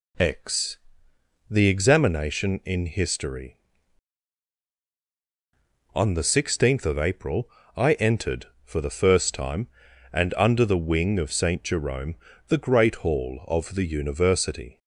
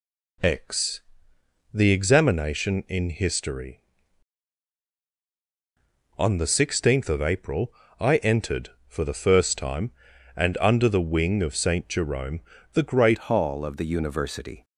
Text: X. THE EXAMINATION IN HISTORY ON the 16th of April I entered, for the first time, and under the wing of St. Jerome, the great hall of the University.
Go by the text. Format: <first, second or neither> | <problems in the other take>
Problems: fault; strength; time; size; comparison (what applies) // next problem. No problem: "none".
first | pauses between "April" and "I"; slight; at 7.7 s; 0.26 s long; slight in the first // changes voice at "hall"; from 13.3 s on; 1.3 s long